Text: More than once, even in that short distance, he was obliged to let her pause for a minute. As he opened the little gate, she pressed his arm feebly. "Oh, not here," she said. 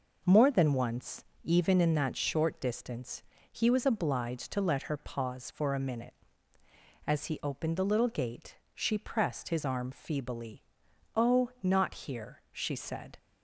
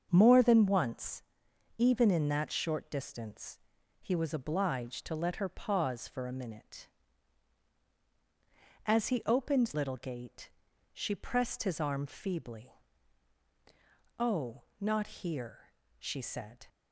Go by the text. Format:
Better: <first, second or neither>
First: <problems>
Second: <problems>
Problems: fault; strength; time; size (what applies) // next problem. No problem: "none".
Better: first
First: none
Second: starts louder than the rest; until 1.1 s; 6.5 dB // skips "the"; at 9.7 s // pauses between "not" and "here"; slight; at 15.0 s; 0.16 s long